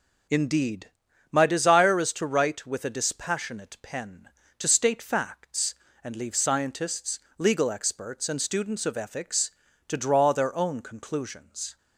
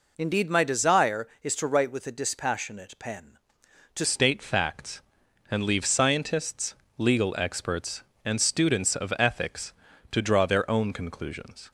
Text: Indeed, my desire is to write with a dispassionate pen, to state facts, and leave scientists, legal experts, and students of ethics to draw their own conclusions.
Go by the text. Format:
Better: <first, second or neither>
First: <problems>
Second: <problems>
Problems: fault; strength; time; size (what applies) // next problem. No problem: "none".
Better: first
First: none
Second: changes voice at "state"; from 4.0 s on; 7.7 s long